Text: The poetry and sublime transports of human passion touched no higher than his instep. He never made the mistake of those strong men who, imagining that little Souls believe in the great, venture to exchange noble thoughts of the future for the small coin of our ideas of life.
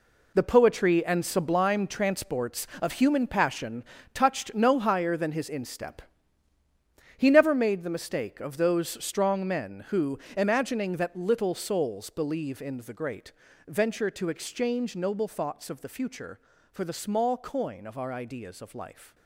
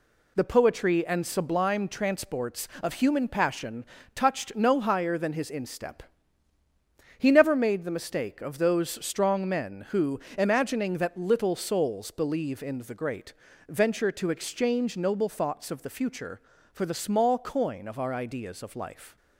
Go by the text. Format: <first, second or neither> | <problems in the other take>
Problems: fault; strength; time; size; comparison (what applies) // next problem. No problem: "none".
second | gets quieter; strong; throughout; 11 dB // pauses between "passion" and "touched"; slight; at 3.8 s; 0.30 s long; slight in the second